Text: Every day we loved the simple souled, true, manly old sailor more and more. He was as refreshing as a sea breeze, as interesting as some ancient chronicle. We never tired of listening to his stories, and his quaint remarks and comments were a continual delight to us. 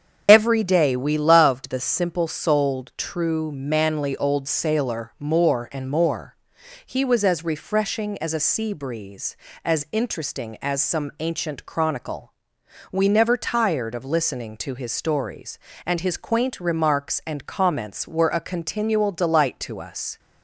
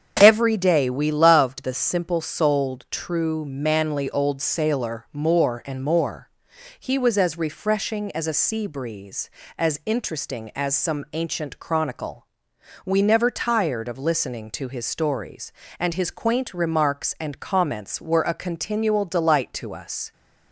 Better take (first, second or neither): second